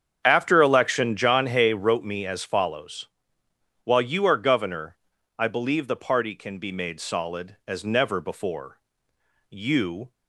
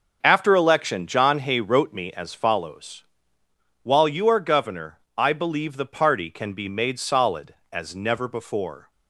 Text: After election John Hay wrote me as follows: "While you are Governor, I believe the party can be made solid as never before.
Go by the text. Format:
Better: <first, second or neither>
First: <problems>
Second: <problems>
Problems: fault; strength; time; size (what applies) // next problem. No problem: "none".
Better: second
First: starts louder than the rest; strong; until 1.2 s; 8 dB // goes on to say "You"; noticeable; from 9.4 s on; 0.62 s long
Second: starts louder than the rest; until 1.2 s; 6 dB